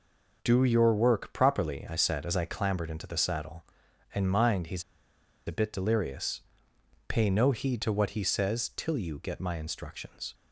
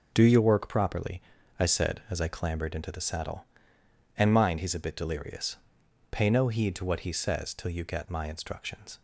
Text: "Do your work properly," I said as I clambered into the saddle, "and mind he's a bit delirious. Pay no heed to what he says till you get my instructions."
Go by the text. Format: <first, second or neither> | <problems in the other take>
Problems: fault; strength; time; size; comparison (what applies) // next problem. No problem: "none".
second | pauses between "he's" and "a"; noticeable; at 4.8 s; 0.64 s long